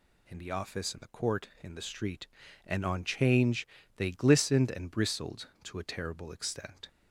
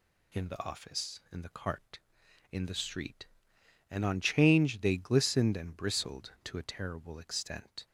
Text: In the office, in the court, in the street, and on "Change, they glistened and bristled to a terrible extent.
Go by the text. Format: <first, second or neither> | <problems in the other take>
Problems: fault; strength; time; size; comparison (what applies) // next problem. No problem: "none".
first | says "cart" for "court"; at 1.5 s